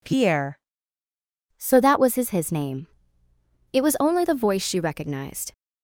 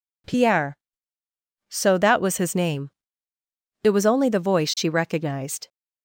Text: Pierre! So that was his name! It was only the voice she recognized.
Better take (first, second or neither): second